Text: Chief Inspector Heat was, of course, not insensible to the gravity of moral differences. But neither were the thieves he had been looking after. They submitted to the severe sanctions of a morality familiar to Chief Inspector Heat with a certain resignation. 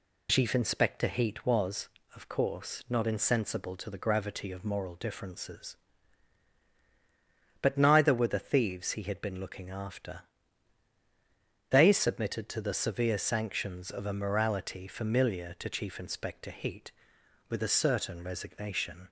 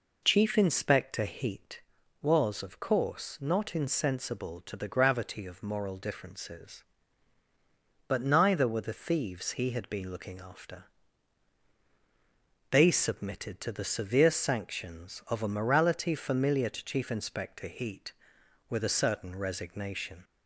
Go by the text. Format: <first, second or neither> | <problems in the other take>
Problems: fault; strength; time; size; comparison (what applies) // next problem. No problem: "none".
neither | none